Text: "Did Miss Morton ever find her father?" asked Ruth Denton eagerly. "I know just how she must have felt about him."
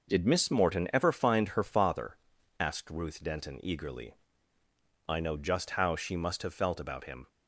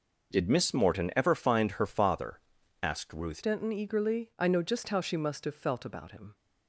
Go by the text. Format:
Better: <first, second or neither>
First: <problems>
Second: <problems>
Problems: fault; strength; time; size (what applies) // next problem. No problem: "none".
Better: first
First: none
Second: changes voice at "Denton"; from 3.4 s on; 2.9 s long